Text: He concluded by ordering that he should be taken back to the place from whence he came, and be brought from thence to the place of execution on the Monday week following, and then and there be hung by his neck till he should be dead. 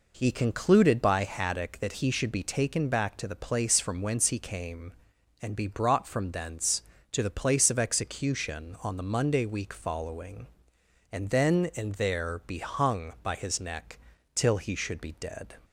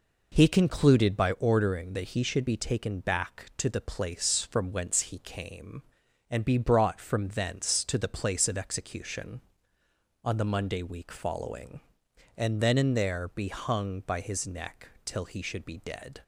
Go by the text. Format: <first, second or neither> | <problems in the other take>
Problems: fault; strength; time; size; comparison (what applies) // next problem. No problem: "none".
second | says "haddock" for "ordering"; at 1.2 s // pauses between "neck" and "till"; slight; at 13.9 s; 0.36 s long; slight in the second